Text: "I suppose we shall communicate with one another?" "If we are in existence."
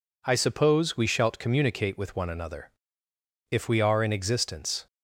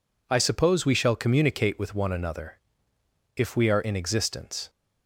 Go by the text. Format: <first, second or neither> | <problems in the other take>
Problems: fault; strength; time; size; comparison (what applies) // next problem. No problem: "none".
second | says "shalt" for "shall"; at 1.0 s